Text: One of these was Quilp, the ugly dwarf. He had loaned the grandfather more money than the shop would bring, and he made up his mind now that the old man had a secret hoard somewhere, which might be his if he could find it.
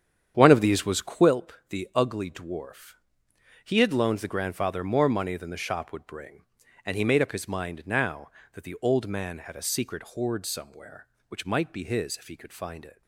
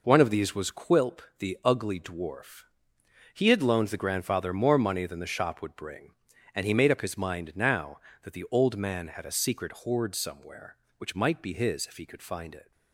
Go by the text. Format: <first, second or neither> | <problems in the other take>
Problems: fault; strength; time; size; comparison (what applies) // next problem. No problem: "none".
second | starts louder than the rest; strong; until 1.4 s; 8.5 dB